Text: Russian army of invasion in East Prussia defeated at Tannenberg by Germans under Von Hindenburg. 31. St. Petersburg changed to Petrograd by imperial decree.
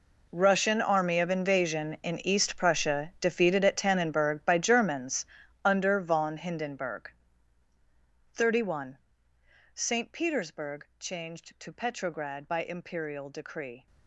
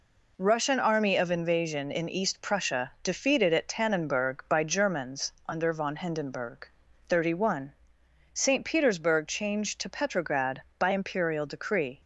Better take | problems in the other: second | gets quieter; strong; throughout; 16 dB // pauses between "Germans" and "under"; at 5.2 s; 0.40 s long; slight in the second

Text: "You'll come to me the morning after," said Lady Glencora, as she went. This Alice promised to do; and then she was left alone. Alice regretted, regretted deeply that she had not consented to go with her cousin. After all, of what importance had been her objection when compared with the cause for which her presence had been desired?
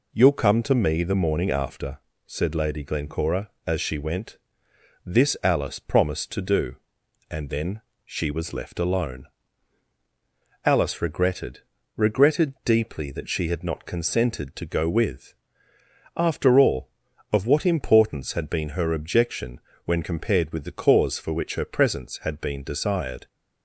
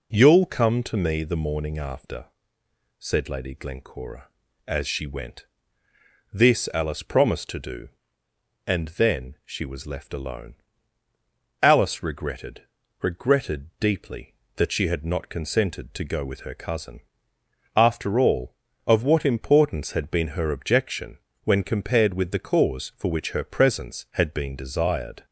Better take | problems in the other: second | pauses between "then" and "she"; slight; at 7.8 s; 0.24 s long // skips "her cousin"; at 15.7 s // pauses between "objection" and "when"; slight; at 19.6 s; 0.24 s long; slight in the second

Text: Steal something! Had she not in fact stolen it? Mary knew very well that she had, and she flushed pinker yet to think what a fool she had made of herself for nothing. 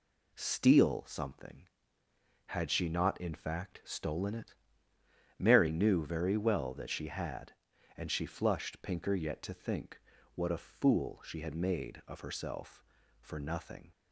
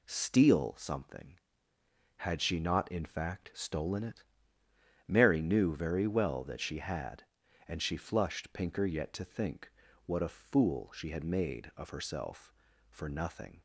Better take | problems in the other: neither | pauses between "think" and "what"; slight; the same in both

